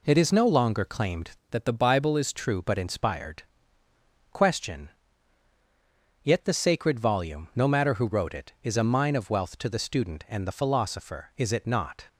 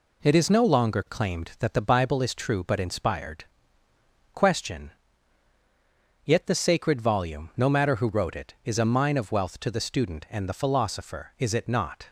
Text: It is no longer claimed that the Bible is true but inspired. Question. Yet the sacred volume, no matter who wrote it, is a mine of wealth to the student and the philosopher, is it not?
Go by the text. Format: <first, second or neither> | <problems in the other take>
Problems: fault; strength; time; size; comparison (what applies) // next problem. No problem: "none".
second | changes voice from "that" to "is"; from 1.5 to 2.3 s; 0.8 s long